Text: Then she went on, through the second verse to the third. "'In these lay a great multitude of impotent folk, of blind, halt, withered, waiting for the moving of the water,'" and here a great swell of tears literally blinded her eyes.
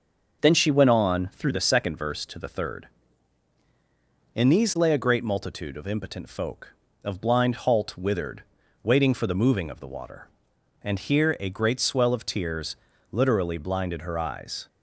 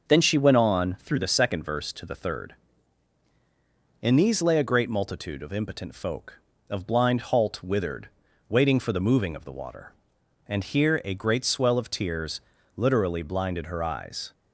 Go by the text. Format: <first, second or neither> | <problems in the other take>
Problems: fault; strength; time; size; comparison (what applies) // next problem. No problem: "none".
neither | starts louder than the rest; the same in both // pauses between "tears" and "literally"; slight; the same in both